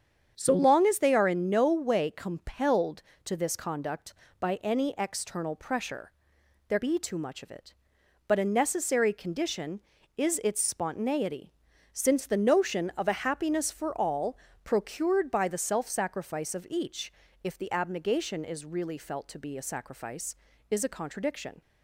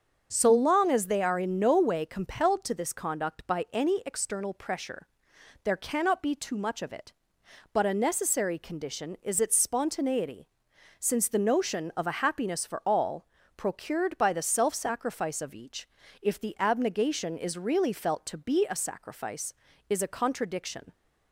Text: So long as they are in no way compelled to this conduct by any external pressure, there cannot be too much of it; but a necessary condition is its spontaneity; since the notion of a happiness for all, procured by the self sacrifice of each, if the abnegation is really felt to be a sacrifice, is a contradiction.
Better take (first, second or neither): second